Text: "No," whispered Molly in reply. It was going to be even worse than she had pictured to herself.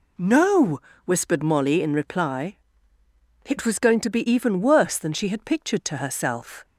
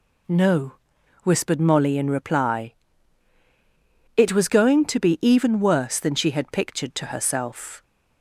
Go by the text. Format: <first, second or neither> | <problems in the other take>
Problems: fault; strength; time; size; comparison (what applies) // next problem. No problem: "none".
neither | none